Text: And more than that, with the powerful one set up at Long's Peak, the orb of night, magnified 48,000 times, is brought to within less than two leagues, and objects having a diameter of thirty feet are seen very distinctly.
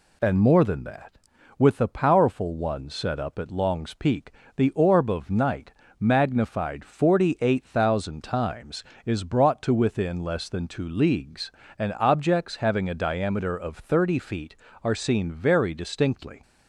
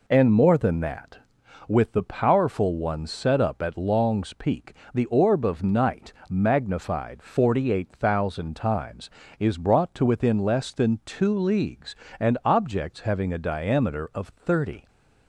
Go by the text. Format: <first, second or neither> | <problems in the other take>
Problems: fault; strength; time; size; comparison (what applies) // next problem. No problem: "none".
first | stops before "feet are seen very distinctly"; at 14.8 s